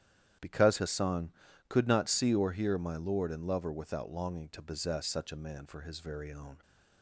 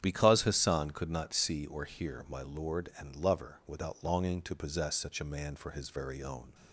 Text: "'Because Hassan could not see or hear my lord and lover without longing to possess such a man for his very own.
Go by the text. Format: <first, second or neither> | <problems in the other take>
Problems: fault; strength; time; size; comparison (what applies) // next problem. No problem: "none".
neither | starts louder than the rest; strong; the same in both